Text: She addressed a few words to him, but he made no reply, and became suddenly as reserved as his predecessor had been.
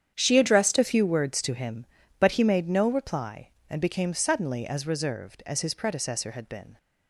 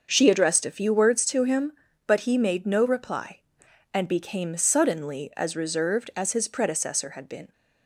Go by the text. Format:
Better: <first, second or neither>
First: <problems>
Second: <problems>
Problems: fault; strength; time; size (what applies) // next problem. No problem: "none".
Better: second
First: starts louder than the rest; strong; until 1.1 s; 8.5 dB // changes voice at "a"; from 0.7 s on; 6.0 s long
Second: starts louder than the rest; until 1.1 s; 6.5 dB